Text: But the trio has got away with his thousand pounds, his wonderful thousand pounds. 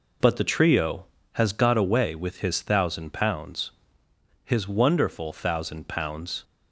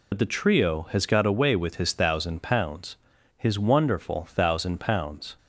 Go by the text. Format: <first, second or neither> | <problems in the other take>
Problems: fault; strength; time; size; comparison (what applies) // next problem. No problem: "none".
first | loses the start of "But"; at 0.1 s; 60 ms